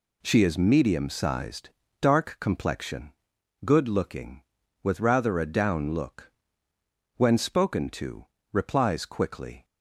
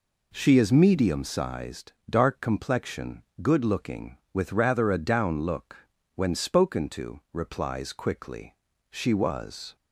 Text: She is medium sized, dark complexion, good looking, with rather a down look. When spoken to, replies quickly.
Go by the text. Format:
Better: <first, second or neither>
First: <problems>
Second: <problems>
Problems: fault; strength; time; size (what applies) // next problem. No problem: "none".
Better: first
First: none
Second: goes on to say "She was"; noticeable; from 8.9 s on; 0.84 s long